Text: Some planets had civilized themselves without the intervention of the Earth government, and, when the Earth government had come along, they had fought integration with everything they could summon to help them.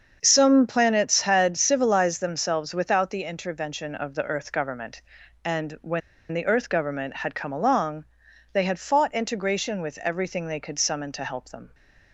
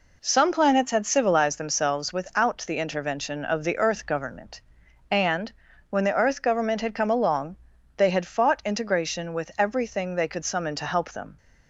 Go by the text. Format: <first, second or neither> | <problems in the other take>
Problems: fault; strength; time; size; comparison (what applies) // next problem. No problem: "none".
second | starts louder than the rest; until 1.2 s; 7 dB // pauses between "when" and "the"; slight; at 6.0 s; 0.31 s long